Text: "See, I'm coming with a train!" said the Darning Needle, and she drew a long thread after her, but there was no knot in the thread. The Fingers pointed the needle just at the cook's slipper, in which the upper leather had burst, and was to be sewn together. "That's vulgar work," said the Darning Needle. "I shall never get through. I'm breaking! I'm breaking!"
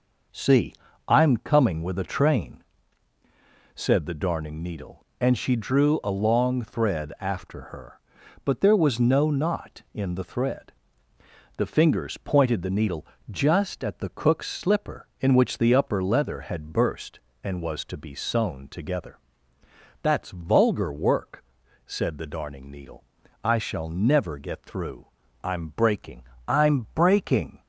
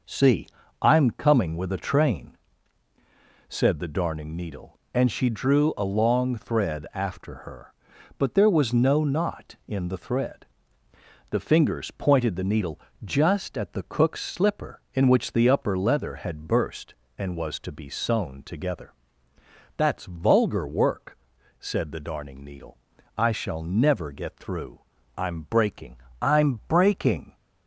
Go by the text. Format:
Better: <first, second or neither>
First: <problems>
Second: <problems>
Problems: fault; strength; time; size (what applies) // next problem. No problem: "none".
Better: neither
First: pauses between "needle" and "just"; slight; at 13.0 s; 0.24 s long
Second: pauses between "needle" and "just"; slight; at 12.7 s; 0.24 s long